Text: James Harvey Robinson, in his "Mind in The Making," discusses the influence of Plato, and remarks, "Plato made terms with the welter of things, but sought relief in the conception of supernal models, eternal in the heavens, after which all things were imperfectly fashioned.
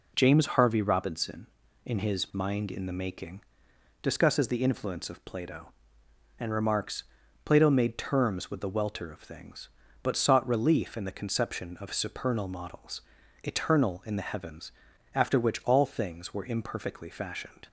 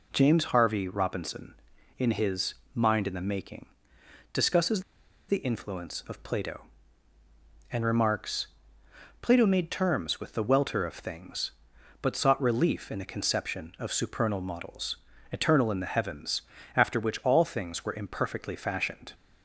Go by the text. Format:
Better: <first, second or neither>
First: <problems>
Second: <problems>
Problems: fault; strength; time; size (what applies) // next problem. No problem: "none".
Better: first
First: none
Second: pauses between "his" and "Mind"; slight; at 2.5 s; 0.18 s long // pauses between "discusses" and "the"; noticeable; at 4.8 s; 0.47 s long